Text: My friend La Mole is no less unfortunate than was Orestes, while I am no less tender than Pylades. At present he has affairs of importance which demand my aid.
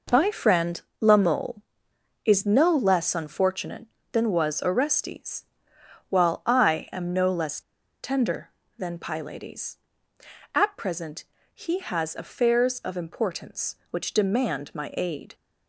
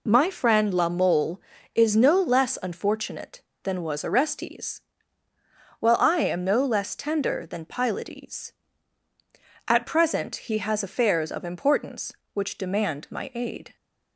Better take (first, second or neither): second